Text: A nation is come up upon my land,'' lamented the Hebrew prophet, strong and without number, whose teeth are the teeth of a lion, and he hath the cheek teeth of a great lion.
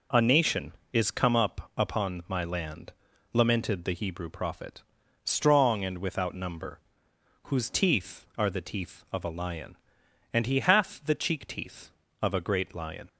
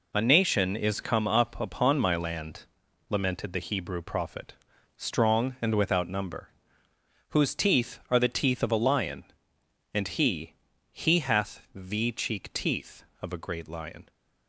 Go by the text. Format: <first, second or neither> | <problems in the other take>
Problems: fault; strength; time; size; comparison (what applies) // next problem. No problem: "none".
first | says "he" twice; at 10.9 s